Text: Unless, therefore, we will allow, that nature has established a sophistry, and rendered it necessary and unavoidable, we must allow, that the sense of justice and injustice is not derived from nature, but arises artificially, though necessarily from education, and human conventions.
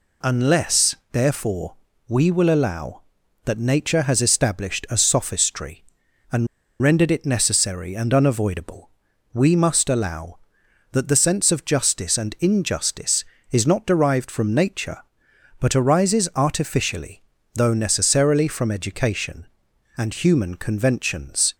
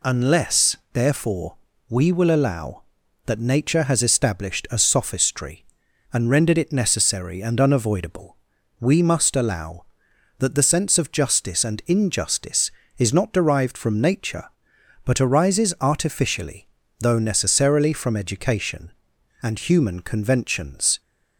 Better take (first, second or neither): second